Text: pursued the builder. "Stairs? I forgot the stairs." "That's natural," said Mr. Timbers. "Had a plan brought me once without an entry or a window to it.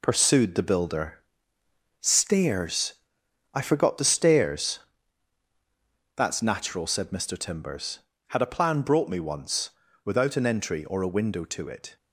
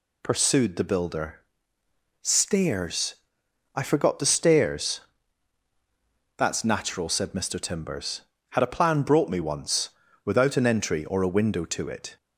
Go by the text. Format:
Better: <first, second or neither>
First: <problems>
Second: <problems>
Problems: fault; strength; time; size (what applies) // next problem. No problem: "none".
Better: second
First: gets quieter; throughout; 7 dB // pauses between "once" and "without"; slight; at 9.7 s; 0.33 s long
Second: pauses between "once" and "without"; slight; at 9.9 s; 0.34 s long